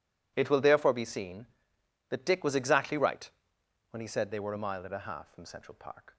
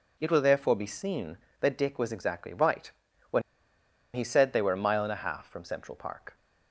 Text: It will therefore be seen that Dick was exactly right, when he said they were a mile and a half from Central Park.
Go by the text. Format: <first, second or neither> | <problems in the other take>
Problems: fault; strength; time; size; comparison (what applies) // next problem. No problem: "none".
first | pauses between "when" and "he"; noticeable; at 3.4 s; 0.73 s long